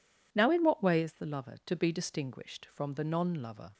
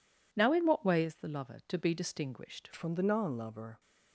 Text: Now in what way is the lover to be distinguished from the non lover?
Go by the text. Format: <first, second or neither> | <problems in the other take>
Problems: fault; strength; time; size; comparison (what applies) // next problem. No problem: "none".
first | changes voice at "from"; from 2.7 s on; 1.0 s long